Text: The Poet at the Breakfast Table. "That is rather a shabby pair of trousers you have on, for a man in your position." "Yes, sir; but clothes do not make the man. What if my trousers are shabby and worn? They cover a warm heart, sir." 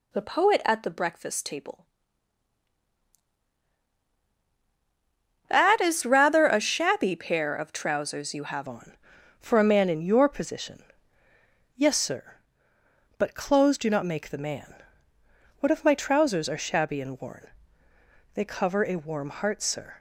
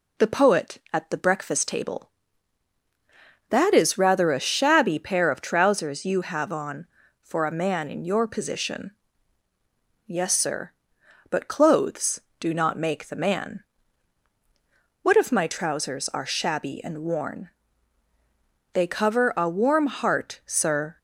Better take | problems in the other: second | changes voice at "on"; from 8.6 s on; 11.3 s long

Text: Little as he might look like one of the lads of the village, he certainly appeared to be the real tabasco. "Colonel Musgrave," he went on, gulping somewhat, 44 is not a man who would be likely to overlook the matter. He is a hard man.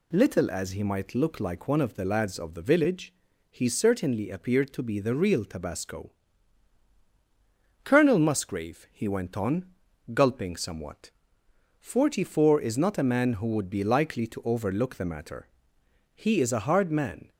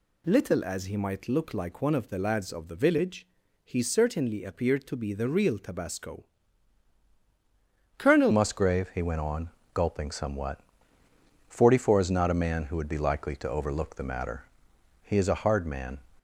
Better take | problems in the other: first | changes voice at "Musgrave"; from 8.3 s on; 7.6 s long

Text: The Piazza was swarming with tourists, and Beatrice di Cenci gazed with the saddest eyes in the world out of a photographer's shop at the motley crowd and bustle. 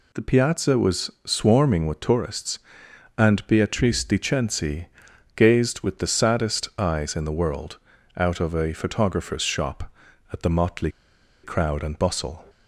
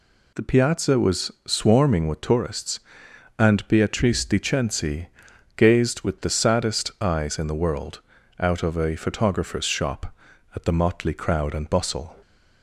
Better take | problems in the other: second | pauses between "Cenci" and "gazed"; noticeable; at 4.8 s; 0.50 s long; noticeable in the second // pauses between "world" and "out"; at 7.7 s; 0.40 s long; also in the second // pauses between "motley" and "crowd"; noticeable; at 10.8 s; 0.53 s long

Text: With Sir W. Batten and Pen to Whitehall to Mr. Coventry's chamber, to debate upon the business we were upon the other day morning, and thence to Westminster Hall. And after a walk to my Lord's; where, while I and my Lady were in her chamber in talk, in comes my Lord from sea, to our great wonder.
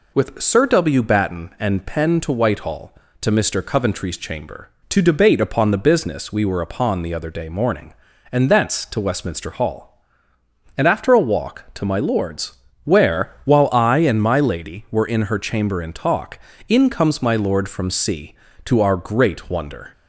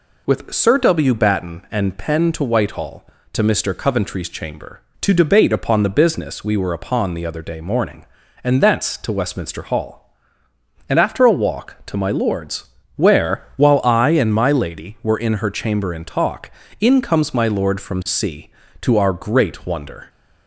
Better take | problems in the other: neither | none

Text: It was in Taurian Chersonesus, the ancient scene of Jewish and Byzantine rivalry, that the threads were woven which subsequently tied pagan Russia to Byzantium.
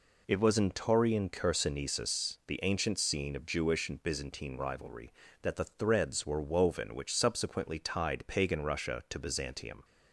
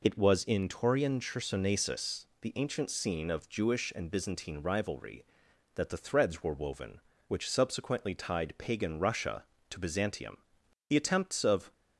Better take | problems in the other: first | goes on to say "The attempts of"; noticeable; from 10.8 s on; 0.84 s long

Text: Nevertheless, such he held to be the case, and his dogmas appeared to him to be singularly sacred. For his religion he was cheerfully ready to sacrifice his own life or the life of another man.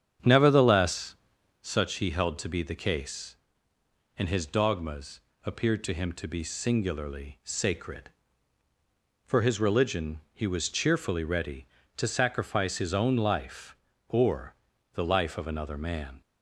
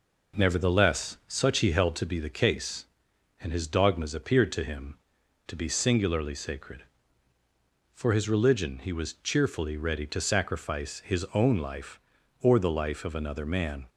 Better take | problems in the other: second | starts louder than the rest; strong; until 1.8 s; 8.5 dB // pauses between "dogmas" and "appeared"; slight; at 5.1 s; 0.26 s long // pauses between "or" and "the"; at 14.5 s; 0.40 s long

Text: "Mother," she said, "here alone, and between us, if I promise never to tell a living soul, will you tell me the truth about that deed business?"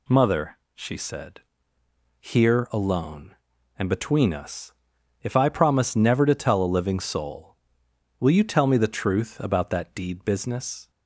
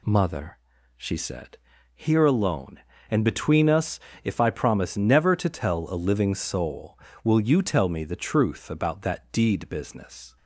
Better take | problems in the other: neither | none

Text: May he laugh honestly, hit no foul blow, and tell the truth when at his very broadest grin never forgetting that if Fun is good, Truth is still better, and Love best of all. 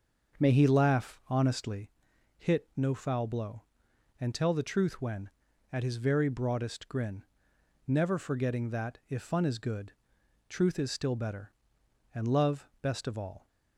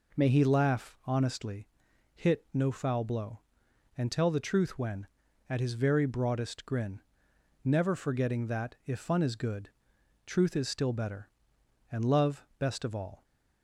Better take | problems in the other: second | starts louder than the rest; until 1.9 s; 6.5 dB // pauses between "grin" and "never"; noticeable; at 7.2 s; 0.62 s long; noticeable in the second

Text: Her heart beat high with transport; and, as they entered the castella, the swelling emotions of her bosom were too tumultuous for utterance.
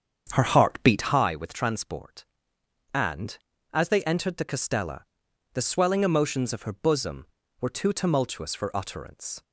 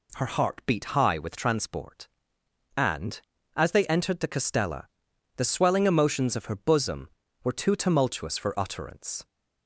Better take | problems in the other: second | starts louder than the rest; strong; until 1.2 s; 7.5 dB

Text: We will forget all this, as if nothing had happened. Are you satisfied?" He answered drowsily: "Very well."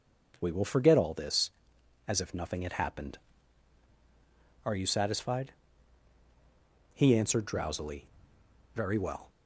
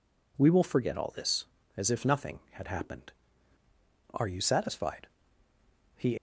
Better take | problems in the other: first | stops before "answered drowsily Very well"; at 6.1 s

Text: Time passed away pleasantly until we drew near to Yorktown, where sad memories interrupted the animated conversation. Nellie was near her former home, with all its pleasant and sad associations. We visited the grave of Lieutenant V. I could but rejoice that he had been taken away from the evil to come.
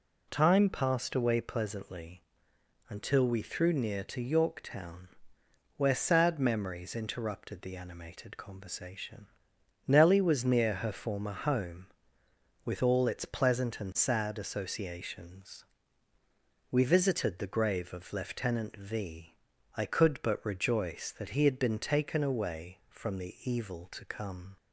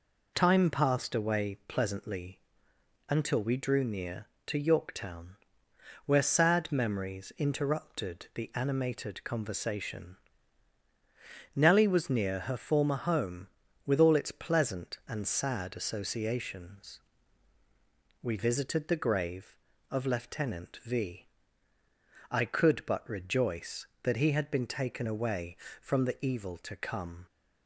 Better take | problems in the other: second | pauses between "pleasantly" and "until"; noticeable; at 2.2 s; 0.68 s long; noticeable in the second // says "threw" for "drew"; at 3.4 s

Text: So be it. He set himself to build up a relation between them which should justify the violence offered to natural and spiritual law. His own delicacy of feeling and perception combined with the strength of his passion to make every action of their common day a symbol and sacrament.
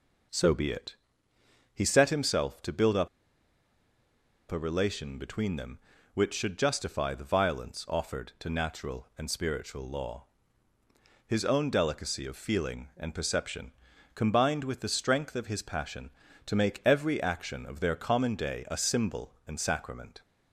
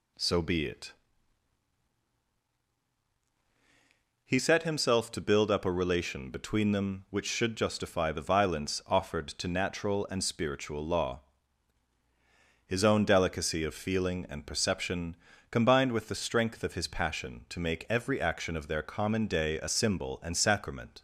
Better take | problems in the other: second | pauses between "up" and "a"; strong; at 3.0 s; 1.4 s long // pauses between "perception" and "combined"; at 13.7 s; 0.44 s long; slight in the second

